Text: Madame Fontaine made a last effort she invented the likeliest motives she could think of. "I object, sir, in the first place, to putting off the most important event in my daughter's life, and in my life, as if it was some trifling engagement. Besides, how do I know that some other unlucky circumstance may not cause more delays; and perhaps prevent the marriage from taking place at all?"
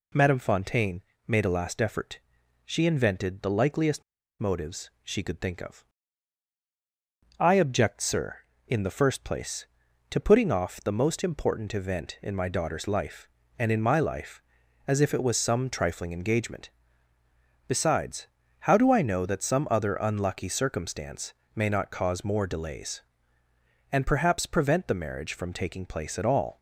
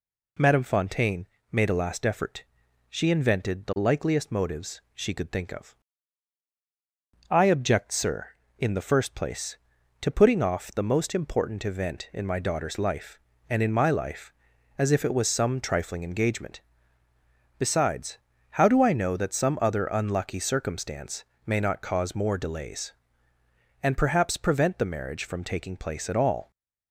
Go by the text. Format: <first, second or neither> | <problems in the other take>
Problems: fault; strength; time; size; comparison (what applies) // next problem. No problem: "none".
second | pauses between "Fontaine" and "made"; slight; at 1.0 s; 0.26 s long; slight in the second // pauses between "effort" and "she"; noticeable; at 2.1 s; 0.46 s long; noticeable in the second // pauses between "likeliest" and "motives"; at 4.0 s; 0.38 s long // pauses between "circumstance" and "may"; slight; at 21.3 s; 0.22 s long; slight in the second